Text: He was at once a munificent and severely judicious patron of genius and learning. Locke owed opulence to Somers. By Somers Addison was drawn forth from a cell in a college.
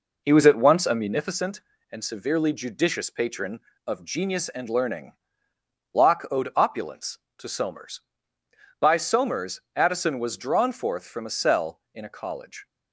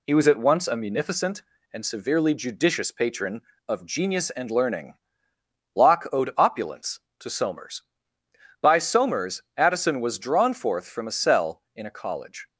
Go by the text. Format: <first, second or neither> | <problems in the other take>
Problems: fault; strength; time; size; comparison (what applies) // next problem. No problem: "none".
second | starts louder than the rest; noticeable; until 1.2 s; 4.5 dB // pauses between "Somers" and "Addison"; slight; at 9.5 s; 0.16 s long; slight in the second